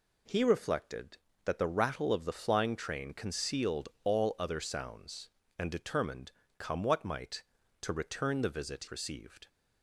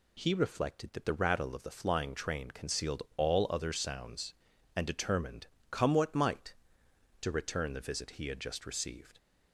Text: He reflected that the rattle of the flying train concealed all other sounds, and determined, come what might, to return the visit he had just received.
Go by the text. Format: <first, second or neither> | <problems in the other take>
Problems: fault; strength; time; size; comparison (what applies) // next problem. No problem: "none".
second | skips "he had just"; at 8.8 s